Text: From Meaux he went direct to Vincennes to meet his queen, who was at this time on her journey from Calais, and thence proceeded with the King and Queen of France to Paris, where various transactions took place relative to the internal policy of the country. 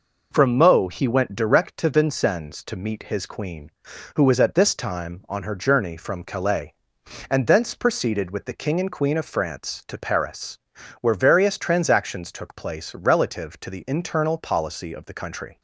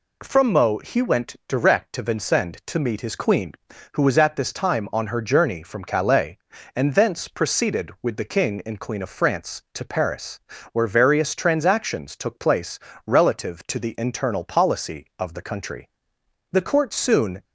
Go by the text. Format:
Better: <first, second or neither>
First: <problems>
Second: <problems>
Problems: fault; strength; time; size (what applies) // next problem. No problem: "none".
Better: first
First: none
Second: pauses between "place" and "relative"; slight; at 12.7 s; 0.26 s long // goes on to say "The court soon"; noticeable; from 16.4 s on; 0.94 s long